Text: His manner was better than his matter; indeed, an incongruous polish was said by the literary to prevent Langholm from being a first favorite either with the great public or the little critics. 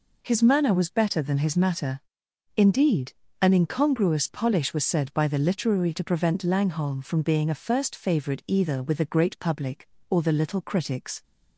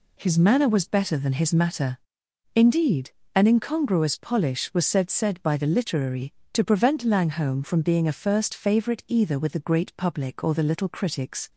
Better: first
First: none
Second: says "said" twice; at 5.1 s

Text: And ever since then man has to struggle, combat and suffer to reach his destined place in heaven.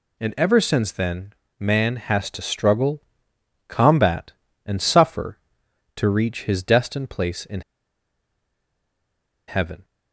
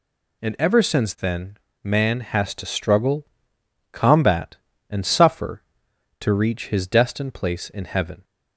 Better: second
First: pauses between "then" and "man"; slight; at 1.3 s; 0.26 s long // pauses between "in" and "heaven"; strong; at 7.6 s; 1.8 s long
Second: pauses between "then" and "man"; slight; at 1.5 s; 0.26 s long

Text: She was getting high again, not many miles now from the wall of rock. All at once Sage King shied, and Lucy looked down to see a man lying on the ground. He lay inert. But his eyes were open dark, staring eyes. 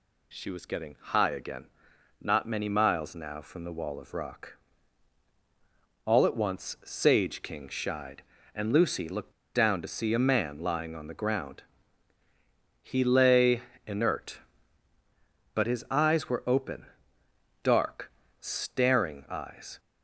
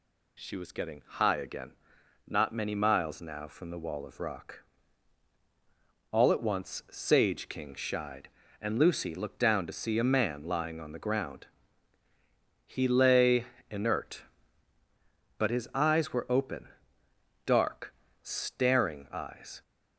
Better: second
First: pauses between "looked" and "down"; slight; at 9.3 s; 0.22 s long // pauses between "lay" and "inert"; slight; at 13.6 s; 0.26 s long // pauses between "open" and "dark"; noticeable; at 16.8 s; 0.78 s long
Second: pauses between "lay" and "inert"; slight; at 13.4 s; 0.26 s long // pauses between "open" and "dark"; noticeable; at 16.6 s; 0.78 s long

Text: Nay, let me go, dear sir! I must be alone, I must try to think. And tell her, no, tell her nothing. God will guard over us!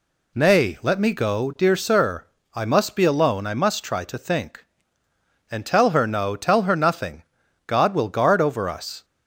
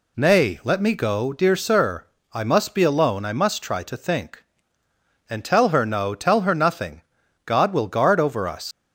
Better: first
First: none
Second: leaves "us" unfinished; at 8.7 s; 120 ms

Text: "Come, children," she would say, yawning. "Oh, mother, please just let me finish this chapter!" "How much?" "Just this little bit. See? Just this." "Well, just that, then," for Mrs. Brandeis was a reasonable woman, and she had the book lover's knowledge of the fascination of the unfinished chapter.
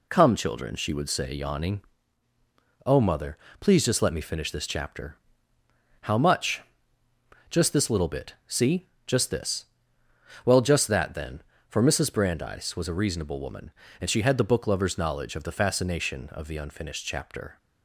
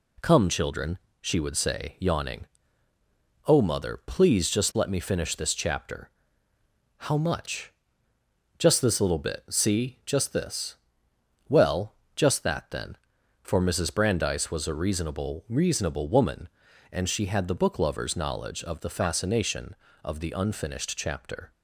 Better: first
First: none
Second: says "reasonable" twice; at 15.4 s

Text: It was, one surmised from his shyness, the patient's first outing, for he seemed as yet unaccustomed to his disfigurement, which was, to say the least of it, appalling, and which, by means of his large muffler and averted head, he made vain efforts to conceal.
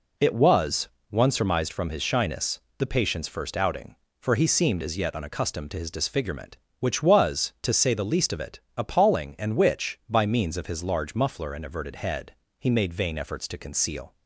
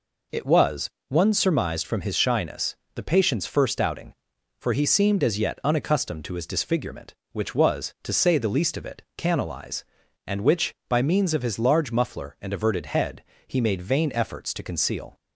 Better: first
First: none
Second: says "canalize" for "appalling"; at 9.1 s

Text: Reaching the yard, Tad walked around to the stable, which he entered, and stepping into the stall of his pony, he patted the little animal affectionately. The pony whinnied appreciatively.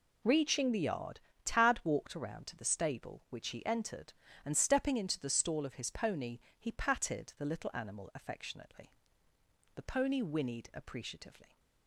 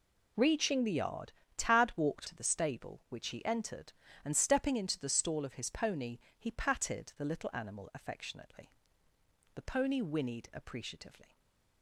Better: first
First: none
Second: skips "around"; at 2.2 s // stays silent after the last word; slight; from 11.2 s on; 0.6 s long

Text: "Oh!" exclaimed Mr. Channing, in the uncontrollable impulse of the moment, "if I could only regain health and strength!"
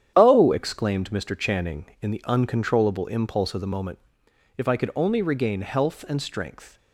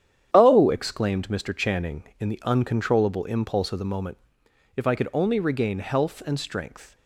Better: neither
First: starts louder than the rest; strong; until 1.1 s; 9 dB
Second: starts louder than the rest; strong; until 1.3 s; 9 dB

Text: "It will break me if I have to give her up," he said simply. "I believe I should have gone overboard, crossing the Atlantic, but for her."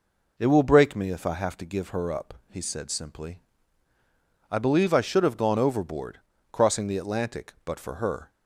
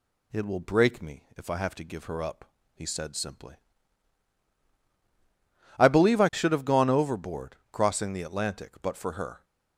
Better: neither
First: none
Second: none

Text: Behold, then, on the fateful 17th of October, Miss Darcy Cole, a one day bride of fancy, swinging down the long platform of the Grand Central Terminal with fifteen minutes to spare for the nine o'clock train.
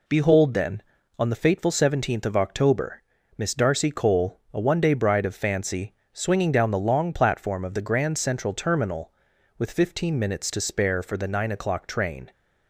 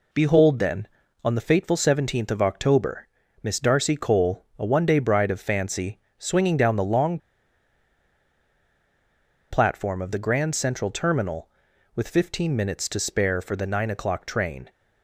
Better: first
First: none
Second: pauses between "long" and "platform"; strong; at 7.1 s; 2.3 s long

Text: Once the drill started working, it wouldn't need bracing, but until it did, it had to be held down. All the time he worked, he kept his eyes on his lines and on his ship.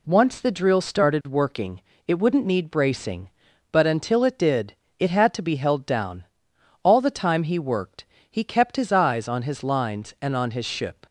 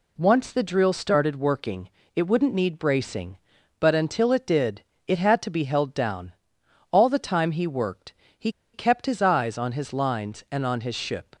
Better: first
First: none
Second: pauses between "he" and "kept"; slight; at 8.4 s; 0.23 s long

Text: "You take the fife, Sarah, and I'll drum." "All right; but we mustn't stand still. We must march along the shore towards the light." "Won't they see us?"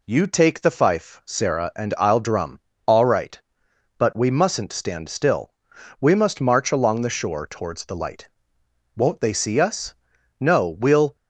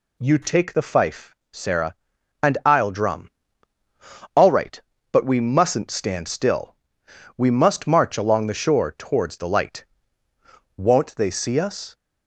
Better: second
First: goes on to say "No we'll"; noticeable; from 10.4 s on; 0.74 s long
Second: none

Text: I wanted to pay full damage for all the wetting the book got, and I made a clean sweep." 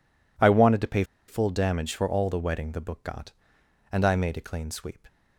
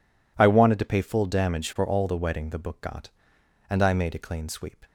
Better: second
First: pauses between "pay" and "full"; slight; at 1.0 s; 0.24 s long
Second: none

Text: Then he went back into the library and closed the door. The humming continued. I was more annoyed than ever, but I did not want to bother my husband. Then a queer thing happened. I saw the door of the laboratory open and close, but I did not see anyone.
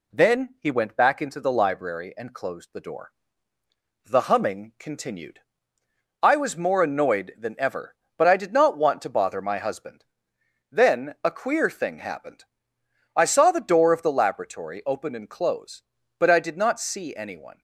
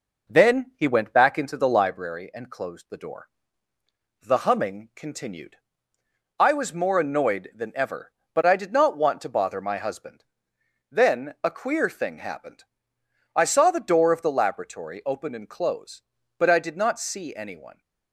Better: first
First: none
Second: starts louder than the rest; noticeable; until 2.0 s; 5 dB

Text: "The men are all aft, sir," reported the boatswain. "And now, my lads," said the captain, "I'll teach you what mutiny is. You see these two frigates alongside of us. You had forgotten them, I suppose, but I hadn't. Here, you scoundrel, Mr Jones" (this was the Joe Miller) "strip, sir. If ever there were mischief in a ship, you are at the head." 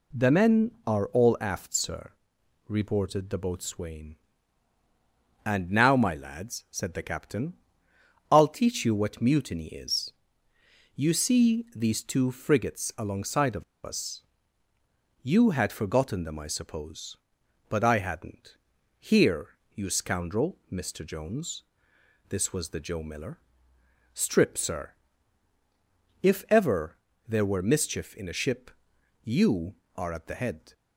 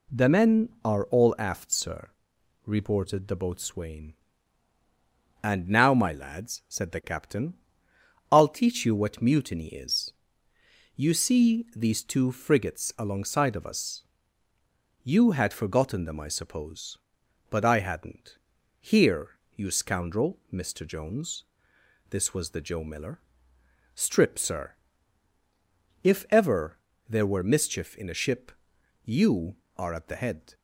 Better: second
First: pauses between "of" and "us"; slight; at 13.6 s; 0.20 s long // pauses between "ever" and "there"; slight; at 26.9 s; 0.32 s long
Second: pauses between "ever" and "there"; slight; at 26.7 s; 0.32 s long

